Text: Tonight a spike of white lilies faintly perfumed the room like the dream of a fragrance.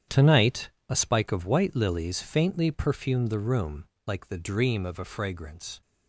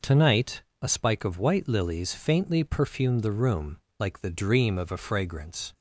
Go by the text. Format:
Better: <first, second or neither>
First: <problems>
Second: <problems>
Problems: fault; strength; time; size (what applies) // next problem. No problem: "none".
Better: second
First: gets quieter; strong; throughout; 12 dB // pauses between "Tonight" and "a"; slight; at 0.7 s; 0.18 s long // pauses between "room" and "like"; slight; at 3.8 s; 0.22 s long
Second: pauses between "Tonight" and "a"; slight; at 0.6 s; 0.18 s long // pauses between "room" and "like"; slight; at 3.7 s; 0.22 s long